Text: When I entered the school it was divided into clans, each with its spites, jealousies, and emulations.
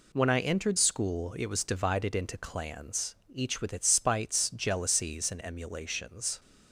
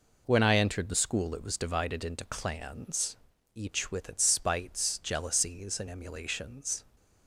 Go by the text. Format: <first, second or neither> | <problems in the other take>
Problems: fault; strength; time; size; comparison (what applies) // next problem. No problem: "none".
second | skips "the"; at 0.7 s